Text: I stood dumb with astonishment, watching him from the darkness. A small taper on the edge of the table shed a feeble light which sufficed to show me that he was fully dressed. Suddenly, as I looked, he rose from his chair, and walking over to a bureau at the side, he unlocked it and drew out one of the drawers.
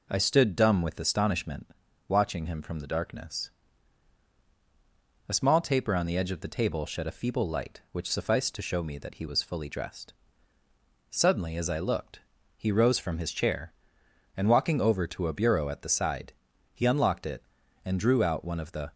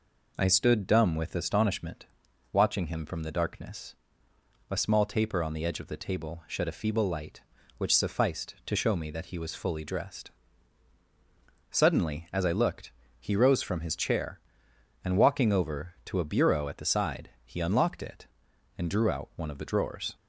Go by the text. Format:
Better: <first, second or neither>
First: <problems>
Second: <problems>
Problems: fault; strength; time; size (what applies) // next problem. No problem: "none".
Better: second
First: stops before "drawers"; at 18.9 s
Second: none